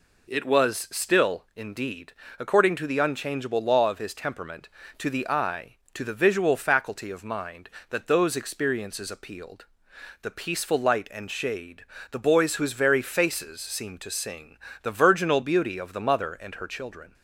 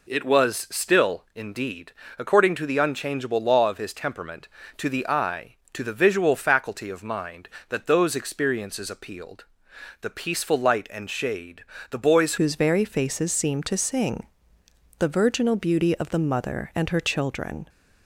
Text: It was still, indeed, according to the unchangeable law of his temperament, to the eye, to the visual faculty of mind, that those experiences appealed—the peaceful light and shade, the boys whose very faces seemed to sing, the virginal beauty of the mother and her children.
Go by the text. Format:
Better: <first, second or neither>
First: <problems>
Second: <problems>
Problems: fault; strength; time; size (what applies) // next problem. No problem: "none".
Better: first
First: none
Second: changes voice at "whose"; from 12.3 s on; 5.3 s long